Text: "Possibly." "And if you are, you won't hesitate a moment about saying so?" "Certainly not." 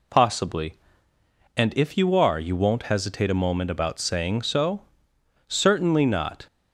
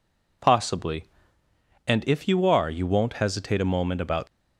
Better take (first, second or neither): first